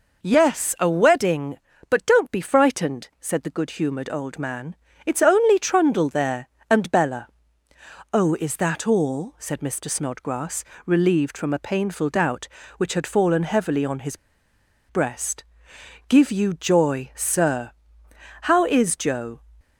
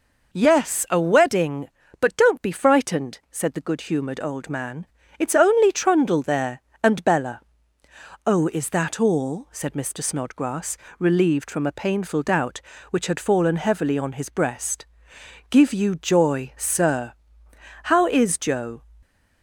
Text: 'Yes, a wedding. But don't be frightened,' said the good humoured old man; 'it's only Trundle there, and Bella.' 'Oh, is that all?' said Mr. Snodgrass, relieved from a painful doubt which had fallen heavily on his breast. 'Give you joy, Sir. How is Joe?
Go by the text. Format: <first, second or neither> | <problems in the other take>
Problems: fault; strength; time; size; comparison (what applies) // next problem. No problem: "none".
second | pauses between "his" and "breast"; noticeable; at 14.1 s; 0.73 s long